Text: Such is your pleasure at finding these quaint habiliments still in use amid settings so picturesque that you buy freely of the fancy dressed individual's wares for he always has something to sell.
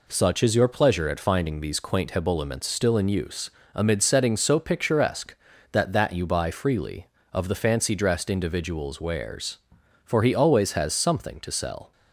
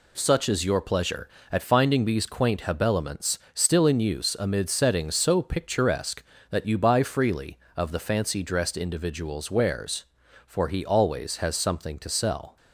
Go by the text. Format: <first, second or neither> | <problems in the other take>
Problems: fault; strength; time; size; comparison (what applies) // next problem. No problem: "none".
second | pauses between "use" and "amid"; slight; at 3.4 s; 0.24 s long // says "that" twice; at 5.9 s